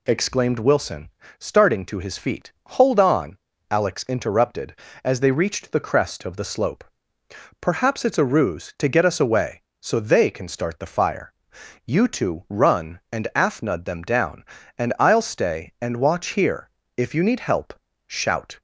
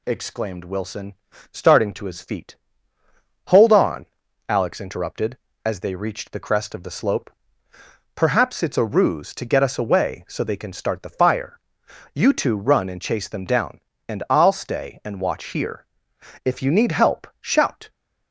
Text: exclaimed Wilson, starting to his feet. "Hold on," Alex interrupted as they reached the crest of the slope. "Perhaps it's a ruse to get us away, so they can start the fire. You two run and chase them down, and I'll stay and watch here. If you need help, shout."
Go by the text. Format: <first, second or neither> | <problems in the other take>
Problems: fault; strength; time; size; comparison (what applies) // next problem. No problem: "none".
second | says "afnud" for "chase"; at 13.3 s